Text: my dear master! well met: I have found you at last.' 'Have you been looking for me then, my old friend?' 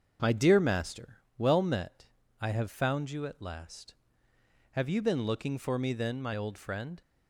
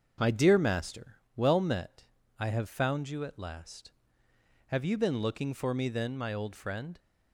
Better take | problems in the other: neither | starts louder than the rest; the same in both

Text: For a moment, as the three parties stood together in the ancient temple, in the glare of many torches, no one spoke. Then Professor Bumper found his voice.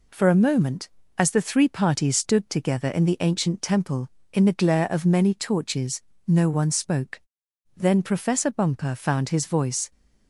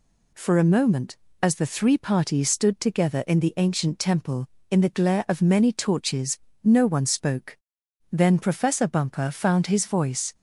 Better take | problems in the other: neither | none

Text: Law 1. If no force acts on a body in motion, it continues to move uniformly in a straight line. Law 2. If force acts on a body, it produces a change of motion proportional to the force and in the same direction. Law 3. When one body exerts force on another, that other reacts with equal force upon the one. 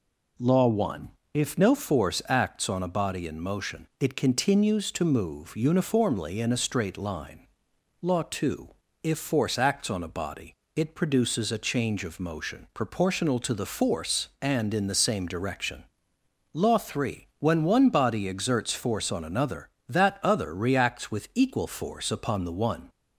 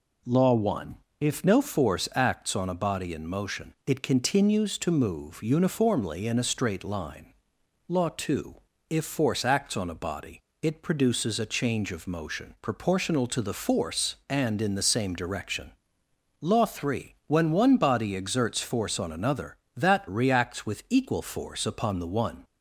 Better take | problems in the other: first | skips "other"; at 20.0 s

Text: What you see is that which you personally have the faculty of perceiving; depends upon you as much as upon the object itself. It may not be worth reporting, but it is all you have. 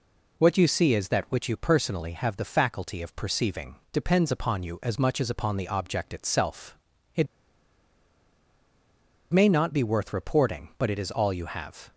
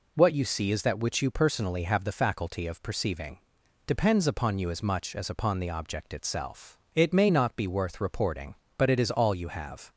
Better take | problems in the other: second | pauses between "It" and "may"; strong; at 7.2 s; 2.0 s long

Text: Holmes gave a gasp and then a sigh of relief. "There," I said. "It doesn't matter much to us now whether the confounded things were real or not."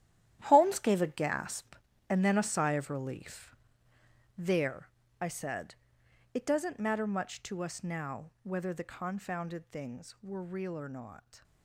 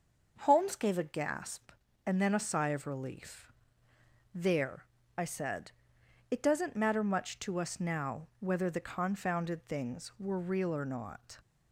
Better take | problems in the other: second | gets quieter; strong; throughout; 12 dB // starts louder than the rest; strong; until 1.4 s; 11.5 dB; noticeable in the second

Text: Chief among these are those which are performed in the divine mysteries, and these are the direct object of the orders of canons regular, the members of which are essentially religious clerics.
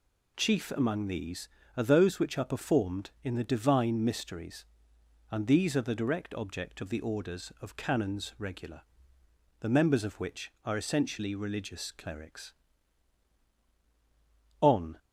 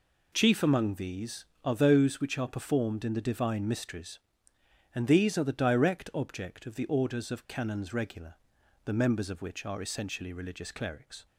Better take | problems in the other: second | goes on to say "On"; slight; from 14.5 s on; 0.38 s long

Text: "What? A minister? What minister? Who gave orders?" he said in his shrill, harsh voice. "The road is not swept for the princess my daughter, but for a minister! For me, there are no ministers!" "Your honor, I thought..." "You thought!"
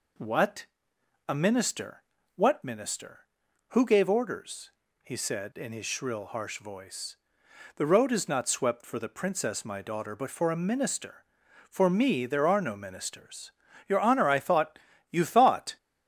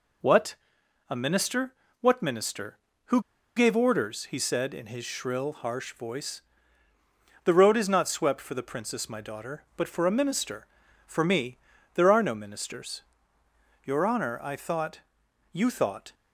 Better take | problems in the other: first | pauses between "Who" and "gave"; at 3.1 s; 0.36 s long

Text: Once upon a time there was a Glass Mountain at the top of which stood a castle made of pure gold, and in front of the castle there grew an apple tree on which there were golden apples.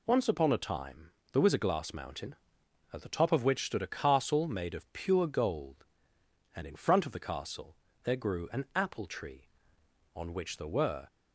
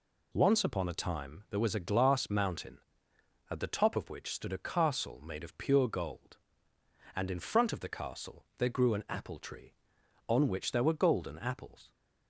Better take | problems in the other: second | pauses between "time" and "there"; slight; at 1.1 s; 0.20 s long // pauses between "castle" and "there"; slight; at 7.7 s; 0.30 s long // stops before "golden apples"; at 11.0 s

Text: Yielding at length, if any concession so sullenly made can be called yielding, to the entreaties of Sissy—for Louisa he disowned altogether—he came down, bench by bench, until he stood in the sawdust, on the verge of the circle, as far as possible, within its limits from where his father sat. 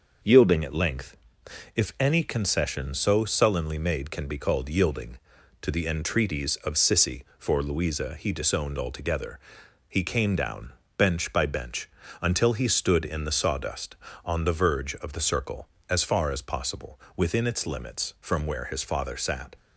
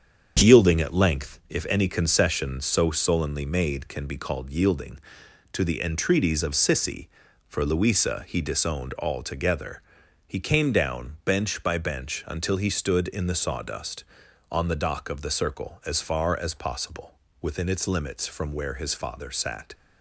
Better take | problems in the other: first | starts louder than the rest; until 1.5 s; 7 dB // says "dock" for "verge"; at 14.7 s

